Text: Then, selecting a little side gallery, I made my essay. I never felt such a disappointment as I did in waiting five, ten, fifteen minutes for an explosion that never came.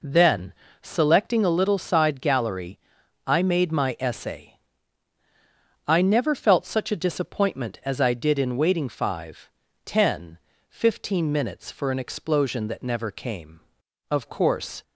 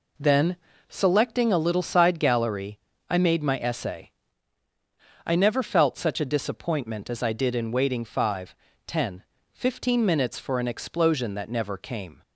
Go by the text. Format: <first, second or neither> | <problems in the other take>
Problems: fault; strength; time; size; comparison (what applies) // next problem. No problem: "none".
second | goes on to say "Of course"; noticeable; from 14.1 s on; 0.72 s long